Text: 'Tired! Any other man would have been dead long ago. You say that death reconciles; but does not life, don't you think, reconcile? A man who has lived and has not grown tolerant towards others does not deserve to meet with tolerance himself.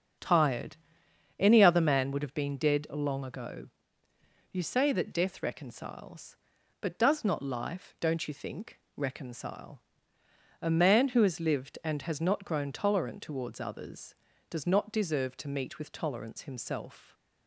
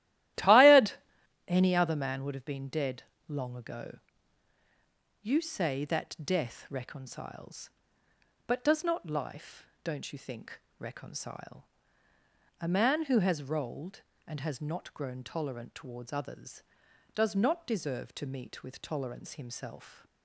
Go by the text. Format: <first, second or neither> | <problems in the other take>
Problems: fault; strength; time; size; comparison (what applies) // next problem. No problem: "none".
first | starts louder than the rest; strong; until 1.9 s; 14.5 dB; also in the first // pauses between "dead" and "long"; slight; at 3.0 s; 0.24 s long // says "rolled" for "lived"; at 13.4 s